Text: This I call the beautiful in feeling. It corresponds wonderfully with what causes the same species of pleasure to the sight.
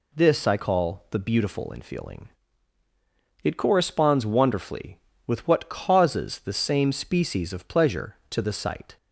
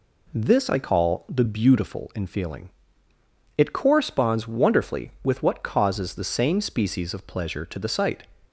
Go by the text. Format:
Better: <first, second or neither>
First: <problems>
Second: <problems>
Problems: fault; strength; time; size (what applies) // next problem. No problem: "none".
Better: neither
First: none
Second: none